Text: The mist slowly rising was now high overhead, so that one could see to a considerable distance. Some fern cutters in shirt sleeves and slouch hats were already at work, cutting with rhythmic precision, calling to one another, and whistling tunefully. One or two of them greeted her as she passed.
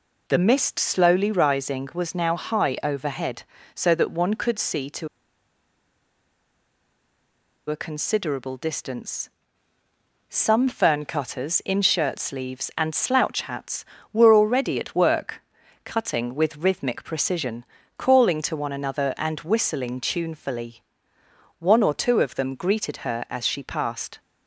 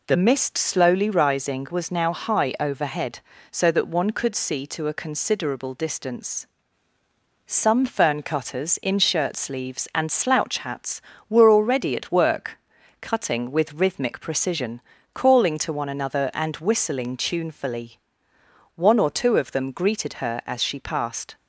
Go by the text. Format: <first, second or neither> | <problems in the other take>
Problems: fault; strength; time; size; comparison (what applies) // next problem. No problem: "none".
second | pauses between "to" and "a"; strong; at 5.0 s; 2.6 s long